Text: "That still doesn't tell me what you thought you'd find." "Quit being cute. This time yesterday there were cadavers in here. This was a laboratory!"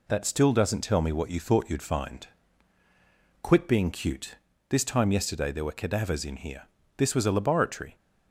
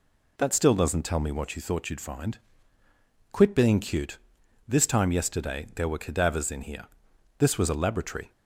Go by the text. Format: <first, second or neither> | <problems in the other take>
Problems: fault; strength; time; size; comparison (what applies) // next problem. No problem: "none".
neither | none